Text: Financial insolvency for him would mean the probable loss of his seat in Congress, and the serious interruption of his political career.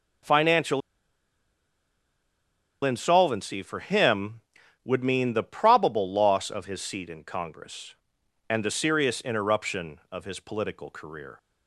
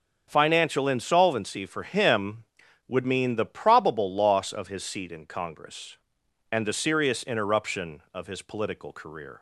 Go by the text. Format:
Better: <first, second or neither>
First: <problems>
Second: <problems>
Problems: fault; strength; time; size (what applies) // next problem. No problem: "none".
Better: second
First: starts louder than the rest; until 3.2 s; 6 dB // pauses between "Financial" and "insolvency"; strong; at 0.8 s; 2.0 s long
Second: starts louder than the rest; until 1.2 s; 6.5 dB